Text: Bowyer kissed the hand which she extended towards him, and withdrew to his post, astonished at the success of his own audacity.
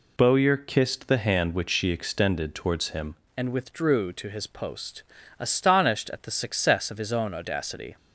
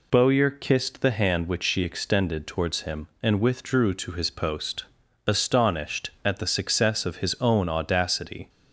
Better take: second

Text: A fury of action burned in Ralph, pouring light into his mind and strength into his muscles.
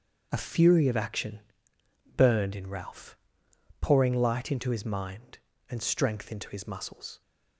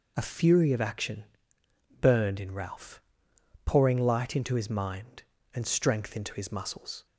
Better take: second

